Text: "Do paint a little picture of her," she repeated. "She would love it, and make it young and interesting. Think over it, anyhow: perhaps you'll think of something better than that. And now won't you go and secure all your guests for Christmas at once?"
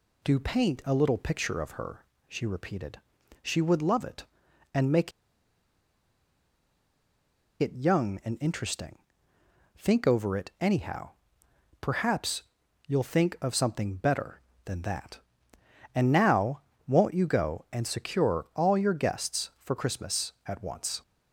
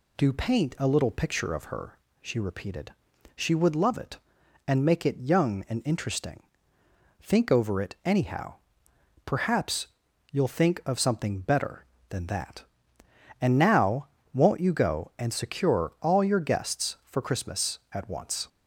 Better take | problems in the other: second | pauses between "make" and "it"; strong; at 5.1 s; 2.4 s long // pauses between "perhaps" and "you'll"; at 12.4 s; 0.44 s long; also in the second // pauses between "now" and "won't"; slight; at 16.6 s; 0.26 s long; slight in the second

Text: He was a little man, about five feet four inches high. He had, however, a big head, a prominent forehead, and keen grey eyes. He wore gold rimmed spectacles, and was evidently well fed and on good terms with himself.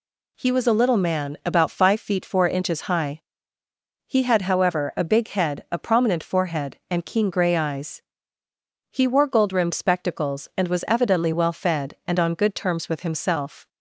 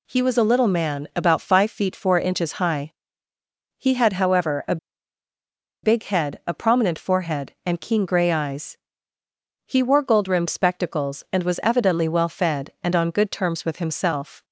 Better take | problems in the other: first | pauses between "a" and "big"; at 4.7 s; 1.0 s long

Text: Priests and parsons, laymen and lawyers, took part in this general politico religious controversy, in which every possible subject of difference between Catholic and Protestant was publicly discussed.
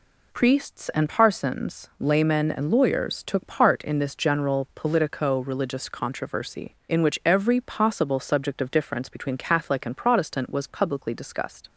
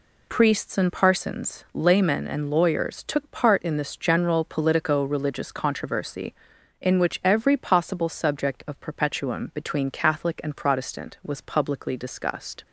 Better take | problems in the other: first | says "perpetuum" for "difference"; at 8.7 s

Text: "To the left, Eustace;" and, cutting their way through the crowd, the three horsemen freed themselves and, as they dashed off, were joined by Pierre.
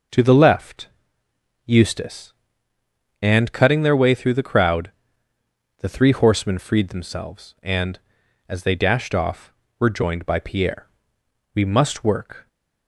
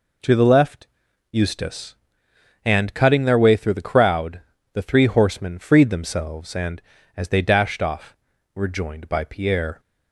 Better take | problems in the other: second | goes on to say "We must work"; noticeable; from 11.5 s on; 0.94 s long

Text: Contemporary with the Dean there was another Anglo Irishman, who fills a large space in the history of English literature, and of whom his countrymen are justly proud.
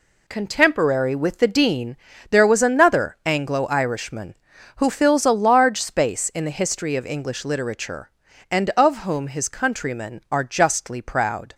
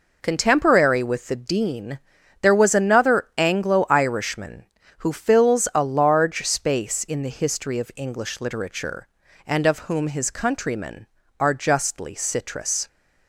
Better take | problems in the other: first | pauses between "Dean" and "there"; at 1.9 s; 0.44 s long; slight in the first // says "citrus" for "proud"; at 12.1 s

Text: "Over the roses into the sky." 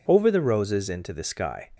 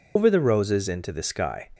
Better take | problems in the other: first | loses the start of "Over"; at 0.1 s; 95 ms

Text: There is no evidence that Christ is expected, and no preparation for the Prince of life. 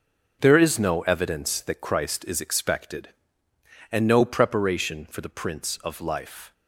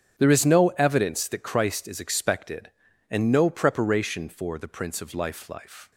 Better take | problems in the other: first | starts louder than the rest; strong; until 1.1 s; 7.5 dB; also in the first // says "life" twice; at 5.4 s

